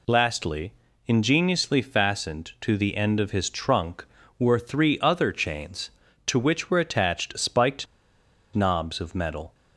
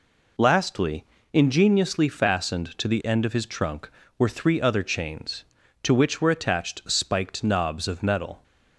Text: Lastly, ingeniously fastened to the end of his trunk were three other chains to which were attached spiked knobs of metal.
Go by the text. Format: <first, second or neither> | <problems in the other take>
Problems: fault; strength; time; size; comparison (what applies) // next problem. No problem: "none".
second | pauses between "spiked" and "knobs"; noticeable; at 7.8 s; 0.70 s long